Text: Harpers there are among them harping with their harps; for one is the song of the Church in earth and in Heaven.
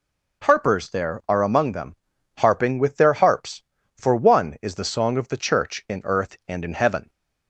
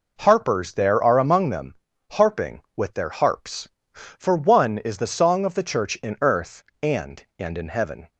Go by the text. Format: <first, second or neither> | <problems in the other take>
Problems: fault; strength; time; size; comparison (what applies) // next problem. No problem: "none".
first | pauses between "them" and "harping"; at 1.7 s; 0.38 s long; also in the first // says "and" twice; at 7.3 s